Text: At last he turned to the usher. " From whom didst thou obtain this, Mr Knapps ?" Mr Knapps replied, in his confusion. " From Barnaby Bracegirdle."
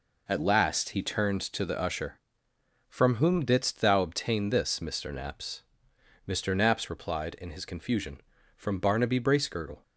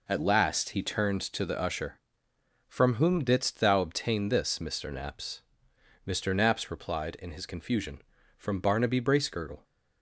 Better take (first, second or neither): neither